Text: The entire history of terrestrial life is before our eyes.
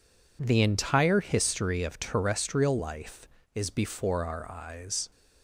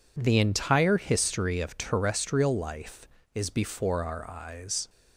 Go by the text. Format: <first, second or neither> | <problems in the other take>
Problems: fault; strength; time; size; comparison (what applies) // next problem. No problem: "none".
neither | none